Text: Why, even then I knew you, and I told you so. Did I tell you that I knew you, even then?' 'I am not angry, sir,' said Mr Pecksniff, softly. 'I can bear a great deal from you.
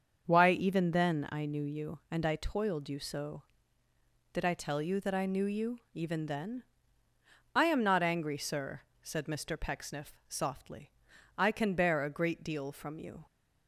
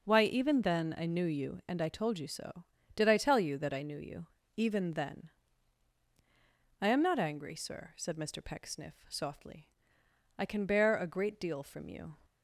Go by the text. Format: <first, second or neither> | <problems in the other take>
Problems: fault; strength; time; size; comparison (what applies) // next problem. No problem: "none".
second | starts louder than the rest; until 1.2 s; 6.5 dB // says "toiled" for "told"; at 2.3 s